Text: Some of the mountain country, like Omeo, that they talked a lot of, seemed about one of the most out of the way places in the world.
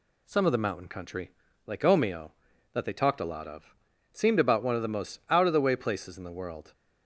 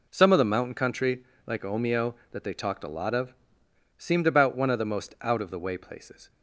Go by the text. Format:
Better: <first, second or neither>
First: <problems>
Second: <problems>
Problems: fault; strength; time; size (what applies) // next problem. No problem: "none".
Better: first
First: none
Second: stops before "in the world"; at 6.2 s